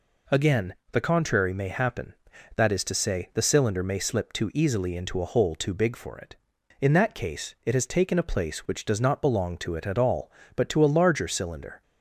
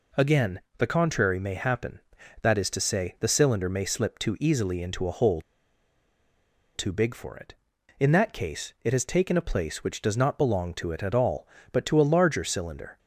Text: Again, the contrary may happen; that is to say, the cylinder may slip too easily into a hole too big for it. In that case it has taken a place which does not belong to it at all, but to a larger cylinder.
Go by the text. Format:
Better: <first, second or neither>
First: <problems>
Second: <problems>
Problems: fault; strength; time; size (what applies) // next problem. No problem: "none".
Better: first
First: none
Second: pauses between "hole" and "too"; strong; at 5.3 s; 1.3 s long